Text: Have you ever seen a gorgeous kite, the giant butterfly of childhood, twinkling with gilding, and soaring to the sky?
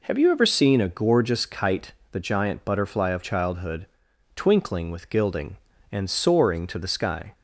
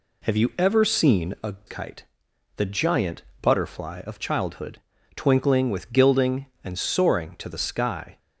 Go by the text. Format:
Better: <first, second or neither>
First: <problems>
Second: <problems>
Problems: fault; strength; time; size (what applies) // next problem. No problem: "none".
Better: first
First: none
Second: skips "gorgeous"; at 1.6 s // pauses between "giant" and "butterfly"; slight; at 3.2 s; 0.18 s long